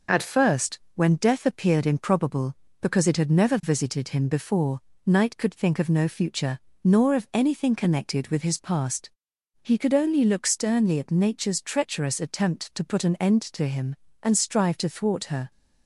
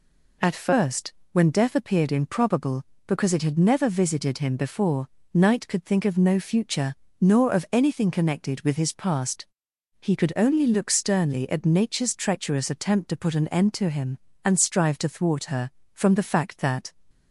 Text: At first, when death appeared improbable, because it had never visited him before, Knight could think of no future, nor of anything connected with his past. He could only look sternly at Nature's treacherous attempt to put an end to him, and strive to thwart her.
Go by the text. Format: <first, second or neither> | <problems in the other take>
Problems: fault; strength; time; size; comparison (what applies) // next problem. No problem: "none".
first | goes on to say "From the fact that"; noticeable; from 15.9 s on; 0.96 s long